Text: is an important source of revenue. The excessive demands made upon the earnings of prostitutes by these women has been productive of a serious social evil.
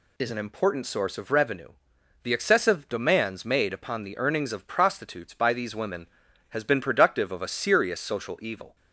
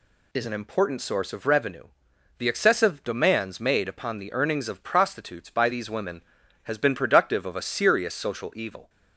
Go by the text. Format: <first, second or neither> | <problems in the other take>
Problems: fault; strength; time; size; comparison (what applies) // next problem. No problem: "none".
neither | none